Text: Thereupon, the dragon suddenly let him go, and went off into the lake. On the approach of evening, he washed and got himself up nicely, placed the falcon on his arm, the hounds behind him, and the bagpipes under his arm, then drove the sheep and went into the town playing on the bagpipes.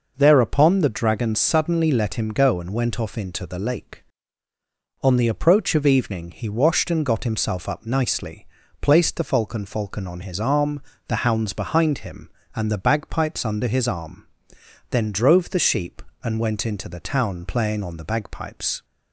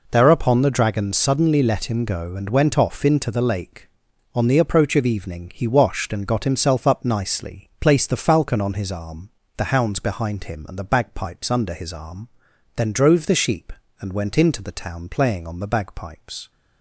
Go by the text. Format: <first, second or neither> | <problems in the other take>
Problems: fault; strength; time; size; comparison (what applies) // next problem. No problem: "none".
second | says "falcon" twice; at 9.6 s